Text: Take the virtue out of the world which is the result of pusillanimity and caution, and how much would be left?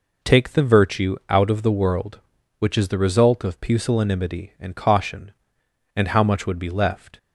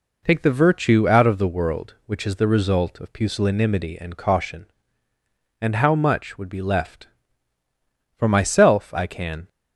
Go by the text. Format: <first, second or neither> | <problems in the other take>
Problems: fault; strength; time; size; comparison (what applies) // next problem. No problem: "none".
first | goes on to say "For myself I can"; noticeable; from 8.1 s on; 1.3 s long